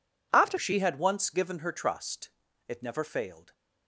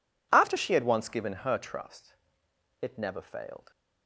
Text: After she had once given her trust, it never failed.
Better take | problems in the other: second | changes voice at "she"; from 0.5 s on; 3.0 s long

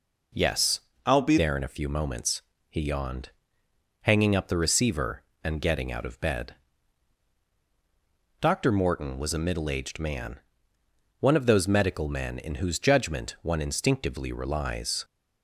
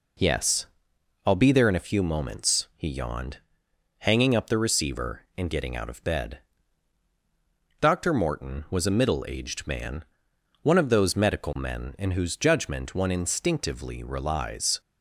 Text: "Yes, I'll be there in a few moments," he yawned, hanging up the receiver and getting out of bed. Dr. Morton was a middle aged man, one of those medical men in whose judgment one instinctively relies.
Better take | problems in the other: second | changes voice from "I'll" to "be"; from 1.0 to 1.3 s; 0.3 s long

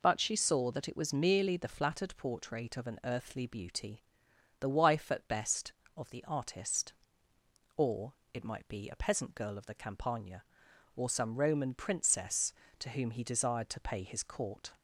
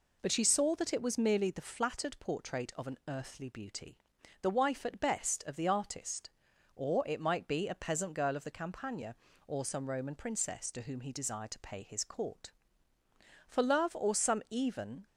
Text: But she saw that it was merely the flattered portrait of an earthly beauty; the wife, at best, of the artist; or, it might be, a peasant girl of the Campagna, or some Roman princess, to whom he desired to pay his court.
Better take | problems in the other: first | goes on to say "For love or some even"; from 13.4 s on; 1.5 s long

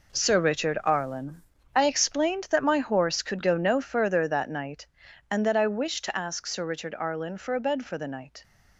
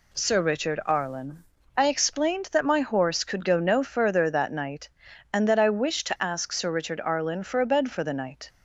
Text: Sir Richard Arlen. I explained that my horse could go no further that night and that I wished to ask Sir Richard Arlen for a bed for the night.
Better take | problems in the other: second | gets quieter; strong; throughout; 10 dB

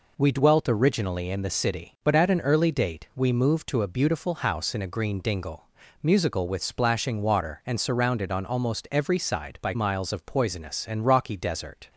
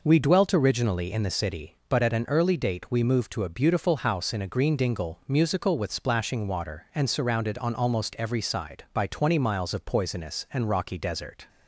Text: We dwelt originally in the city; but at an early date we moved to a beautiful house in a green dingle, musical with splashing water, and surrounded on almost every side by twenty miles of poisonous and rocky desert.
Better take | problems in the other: second | skips "twenty"; at 9.7 s

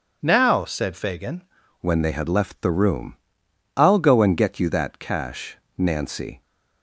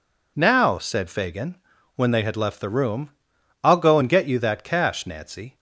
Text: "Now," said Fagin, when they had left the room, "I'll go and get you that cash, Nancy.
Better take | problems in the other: second | changes voice at "when"; from 1.8 s on; 4.6 s long

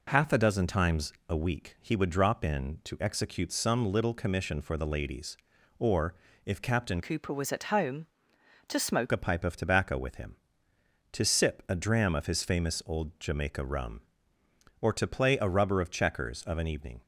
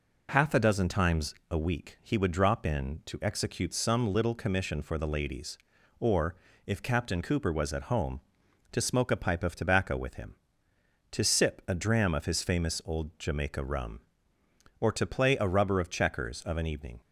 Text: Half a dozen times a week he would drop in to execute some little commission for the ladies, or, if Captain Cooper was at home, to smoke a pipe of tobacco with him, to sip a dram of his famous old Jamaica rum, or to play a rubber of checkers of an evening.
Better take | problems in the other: second | pauses between "times" and "a"; slight; at 1.1 s; 0.16 s long; slight in the second // changes voice from "Cooper" to "smoke"; from 7.0 to 9.0 s; 2.0 s long

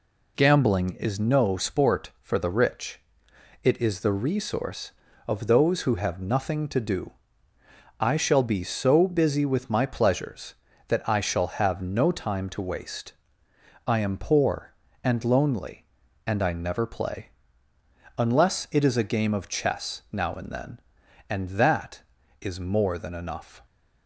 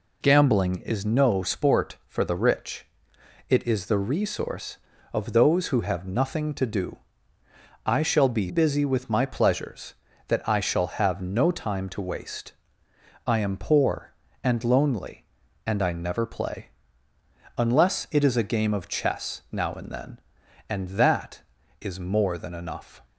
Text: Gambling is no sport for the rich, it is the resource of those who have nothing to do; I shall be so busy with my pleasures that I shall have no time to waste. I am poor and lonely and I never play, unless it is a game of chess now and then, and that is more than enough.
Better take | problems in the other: first | skips "so"; at 8.4 s

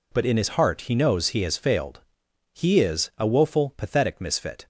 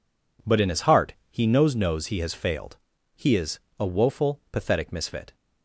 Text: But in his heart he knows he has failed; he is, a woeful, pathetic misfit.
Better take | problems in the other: first | pauses between "heart" and "he"; slight; at 1.1 s; 0.18 s long // says "knows" twice; at 1.7 s

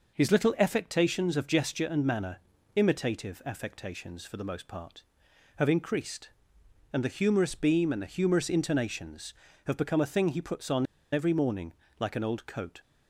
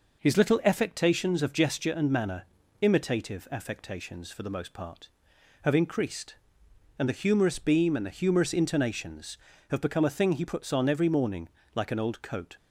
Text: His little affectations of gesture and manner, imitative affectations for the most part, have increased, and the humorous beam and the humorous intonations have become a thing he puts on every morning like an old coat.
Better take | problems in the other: second | pauses between "on" and "every"; slight; at 10.8 s; 0.27 s long // pauses between "morning" and "like"; slight; at 11.7 s; 0.24 s long; slight in the second

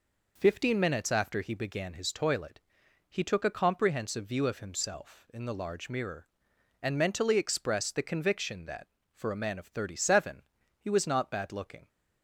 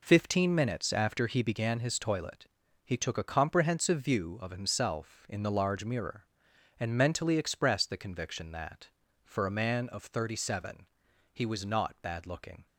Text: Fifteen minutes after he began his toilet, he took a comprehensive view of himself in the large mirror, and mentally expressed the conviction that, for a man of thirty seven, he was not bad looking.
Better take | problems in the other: neither | none

